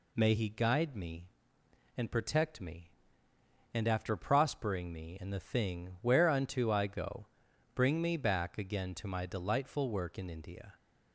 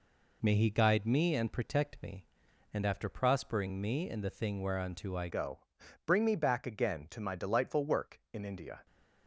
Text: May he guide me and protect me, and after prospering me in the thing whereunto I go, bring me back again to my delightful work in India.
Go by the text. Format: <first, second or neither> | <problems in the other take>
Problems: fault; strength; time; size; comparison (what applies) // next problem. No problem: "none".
first | changes voice at "go"; from 5.2 s on; 3.6 s long